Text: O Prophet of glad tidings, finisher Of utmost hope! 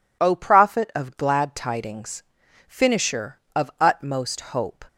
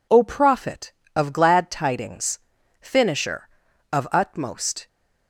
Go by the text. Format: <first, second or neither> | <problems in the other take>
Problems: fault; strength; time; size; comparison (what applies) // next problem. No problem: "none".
first | stops before "hope"; at 4.8 s